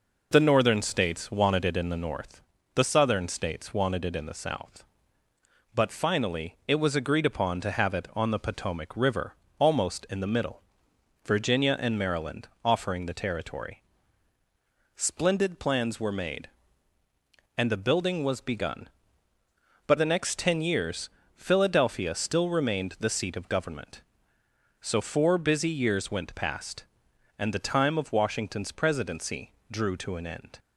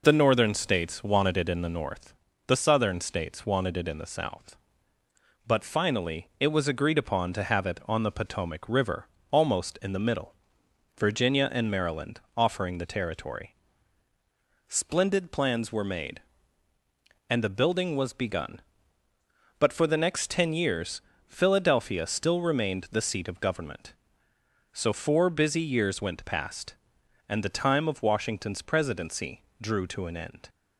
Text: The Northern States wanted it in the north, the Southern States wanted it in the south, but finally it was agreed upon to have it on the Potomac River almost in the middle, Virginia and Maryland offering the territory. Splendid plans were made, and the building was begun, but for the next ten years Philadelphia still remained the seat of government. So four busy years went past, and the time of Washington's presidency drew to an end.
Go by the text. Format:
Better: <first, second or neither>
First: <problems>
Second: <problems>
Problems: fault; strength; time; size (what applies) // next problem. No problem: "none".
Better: second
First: pauses between "River" and "almost"; slight; at 9.3 s; 0.24 s long // pauses between "Maryland" and "offering"; slight; at 12.4 s; 0.16 s long // skips "for"; at 19.9 s // pauses between "years" and "Philadelphia"; slight; at 21.0 s; 0.26 s long // pauses between "presidency" and "drew"; slight; at 29.5 s; 0.18 s long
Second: pauses between "River" and "almost"; slight; at 9.0 s; 0.24 s long // pauses between "Maryland" and "offering"; slight; at 12.2 s; 0.16 s long // pauses between "years" and "Philadelphia"; slight; at 21.0 s; 0.26 s long // pauses between "presidency" and "drew"; slight; at 29.4 s; 0.18 s long